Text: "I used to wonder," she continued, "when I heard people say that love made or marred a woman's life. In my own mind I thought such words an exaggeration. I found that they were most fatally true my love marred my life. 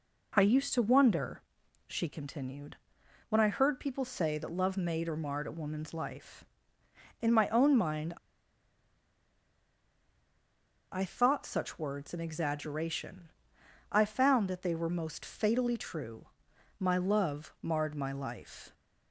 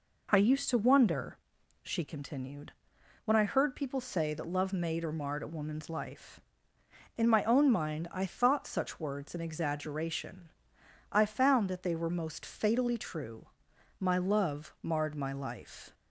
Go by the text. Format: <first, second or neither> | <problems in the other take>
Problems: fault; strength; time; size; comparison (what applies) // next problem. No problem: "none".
second | pauses between "mind" and "I"; strong; at 8.1 s; 2.7 s long // pauses between "true" and "my"; noticeable; at 16.2 s; 0.54 s long; noticeable in the second